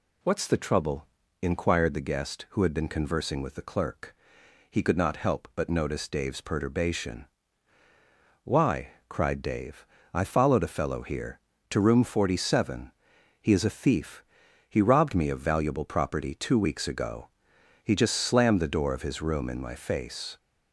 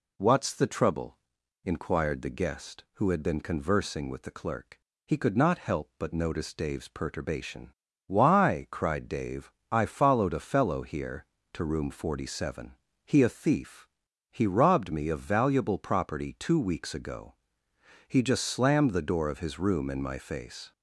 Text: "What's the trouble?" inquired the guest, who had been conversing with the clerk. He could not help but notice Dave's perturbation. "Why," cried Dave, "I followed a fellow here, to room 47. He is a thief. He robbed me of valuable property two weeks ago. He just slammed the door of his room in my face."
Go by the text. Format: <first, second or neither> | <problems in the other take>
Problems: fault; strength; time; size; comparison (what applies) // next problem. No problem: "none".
first | skips "is"; at 13.2 s